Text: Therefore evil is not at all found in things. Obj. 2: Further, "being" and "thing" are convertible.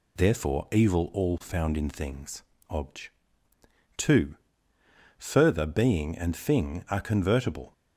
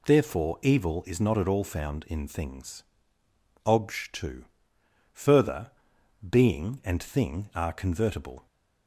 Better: second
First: skips "is not at"; at 1.1 s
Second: none

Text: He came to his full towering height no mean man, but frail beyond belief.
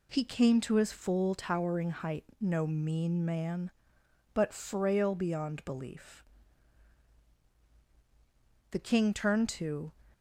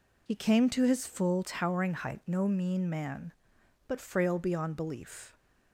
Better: second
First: pauses between "height" and "no"; slight; at 2.2 s; 0.16 s long // goes on to say "The King turned to"; noticeable; from 8.7 s on; 1.2 s long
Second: none

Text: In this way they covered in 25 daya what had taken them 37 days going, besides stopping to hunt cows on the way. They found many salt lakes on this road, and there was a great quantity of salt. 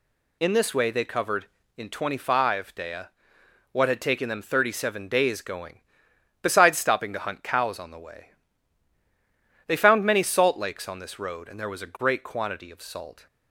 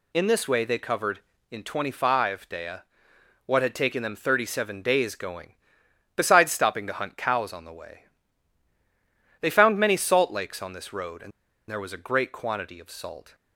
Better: first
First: pauses between "daya" and "what"; noticeable; at 3.0 s; 0.64 s long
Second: pauses between "daya" and "what"; noticeable; at 2.8 s; 0.64 s long // pauses between "and" and "there"; at 11.3 s; 0.38 s long

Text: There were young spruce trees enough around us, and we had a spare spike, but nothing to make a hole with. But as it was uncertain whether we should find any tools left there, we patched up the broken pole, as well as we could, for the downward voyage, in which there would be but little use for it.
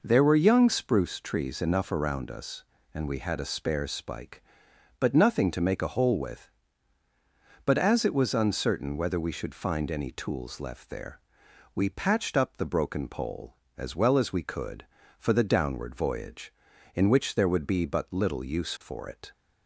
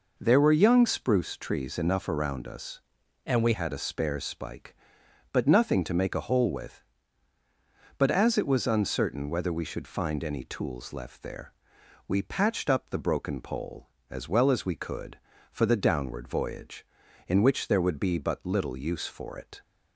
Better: first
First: none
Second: changes voice from "and" to "we"; from 3.2 to 3.5 s; 0.3 s long

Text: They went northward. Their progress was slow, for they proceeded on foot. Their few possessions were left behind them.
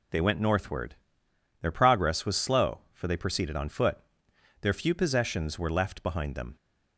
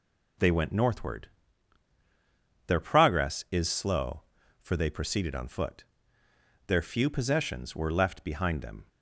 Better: first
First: none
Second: says "is" for "was"; at 3.4 s

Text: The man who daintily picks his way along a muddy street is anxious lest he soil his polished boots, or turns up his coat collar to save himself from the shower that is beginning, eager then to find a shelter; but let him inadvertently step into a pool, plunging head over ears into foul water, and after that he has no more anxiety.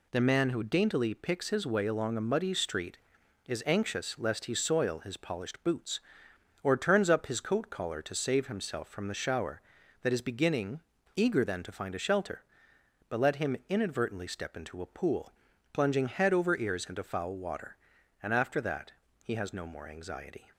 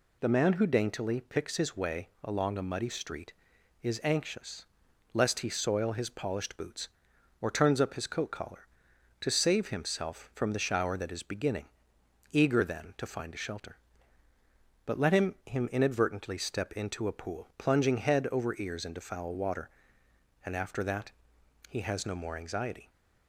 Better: first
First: pauses between "that" and "he"; slight; at 18.9 s; 0.32 s long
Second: pauses between "way" and "along"; slight; at 2.0 s; 0.16 s long // pauses between "anxious" and "lest"; noticeable; at 4.6 s; 0.48 s long // says "him" twice; at 15.4 s // pauses between "that" and "he"; noticeable; at 21.1 s; 0.58 s long

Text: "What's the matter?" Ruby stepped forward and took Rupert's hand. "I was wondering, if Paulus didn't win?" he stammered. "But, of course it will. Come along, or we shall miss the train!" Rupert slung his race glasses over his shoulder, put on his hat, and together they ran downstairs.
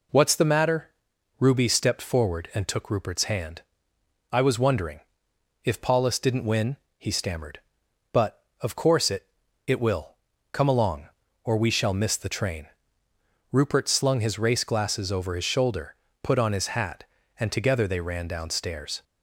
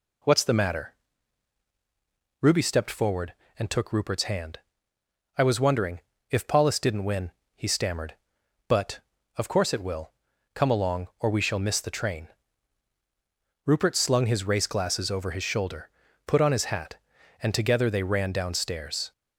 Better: second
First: says "it" twice; at 9.6 s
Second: none

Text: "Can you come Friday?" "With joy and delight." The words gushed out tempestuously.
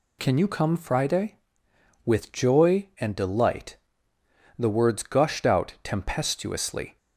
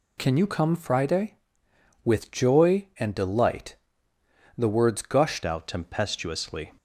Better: first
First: none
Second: changes voice at "out"; from 5.4 s on; 1.3 s long

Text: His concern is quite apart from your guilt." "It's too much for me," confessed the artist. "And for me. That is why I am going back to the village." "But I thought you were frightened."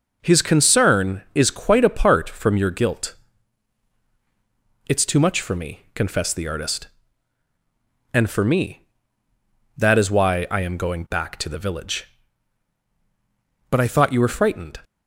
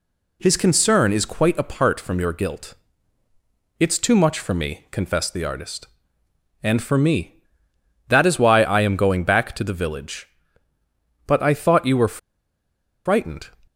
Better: first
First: none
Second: pauses between "were" and "frightened"; noticeable; at 12.1 s; 0.88 s long

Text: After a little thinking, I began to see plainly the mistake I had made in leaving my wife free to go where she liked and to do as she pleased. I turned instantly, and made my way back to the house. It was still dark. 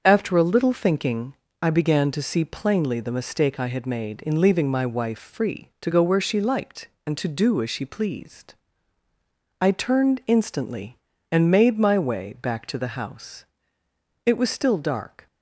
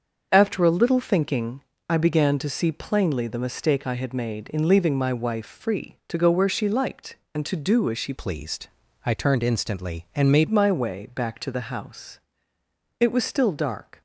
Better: first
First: starts louder than the rest; until 1.0 s; 6.5 dB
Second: starts louder than the rest; until 1.3 s; 6.5 dB // changes voice from "pleased" to "made"; from 8.1 to 10.4 s; 2.3 s long

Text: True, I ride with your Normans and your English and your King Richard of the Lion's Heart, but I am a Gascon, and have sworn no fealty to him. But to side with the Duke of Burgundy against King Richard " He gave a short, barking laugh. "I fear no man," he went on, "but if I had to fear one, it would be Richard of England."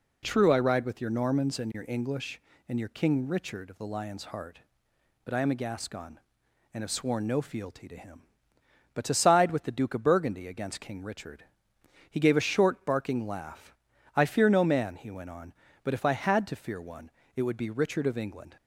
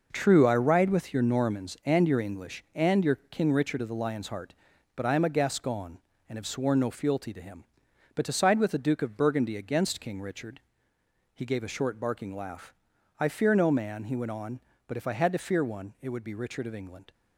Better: first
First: none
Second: gets quieter; strong; throughout; 10 dB

